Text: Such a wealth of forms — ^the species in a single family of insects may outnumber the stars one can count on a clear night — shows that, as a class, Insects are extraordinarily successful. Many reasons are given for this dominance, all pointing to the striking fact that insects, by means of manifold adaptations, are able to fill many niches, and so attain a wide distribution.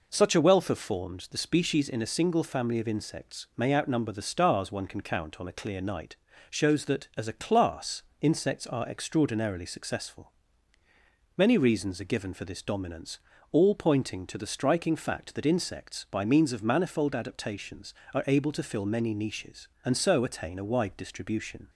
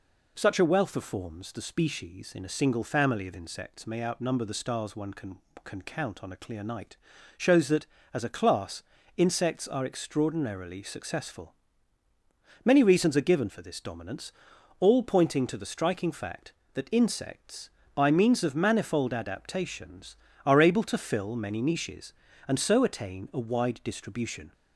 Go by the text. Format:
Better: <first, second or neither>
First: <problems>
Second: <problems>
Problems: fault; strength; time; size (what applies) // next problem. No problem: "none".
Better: first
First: none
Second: says "can" twice; at 5.6 s